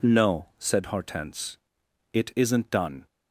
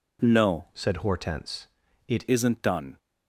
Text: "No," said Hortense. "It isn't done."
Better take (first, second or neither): first